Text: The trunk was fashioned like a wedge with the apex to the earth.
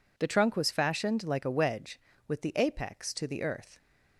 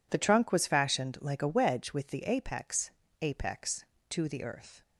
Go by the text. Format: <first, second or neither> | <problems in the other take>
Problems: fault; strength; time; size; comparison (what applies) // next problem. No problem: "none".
first | says "apex" twice; at 3.2 s